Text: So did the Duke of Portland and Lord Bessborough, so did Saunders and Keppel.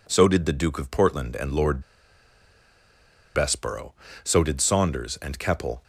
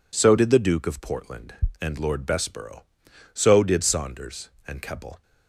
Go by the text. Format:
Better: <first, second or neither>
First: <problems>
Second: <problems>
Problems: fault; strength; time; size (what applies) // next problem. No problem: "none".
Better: second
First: pauses between "Lord" and "Bessborough"; strong; at 1.8 s; 1.5 s long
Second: none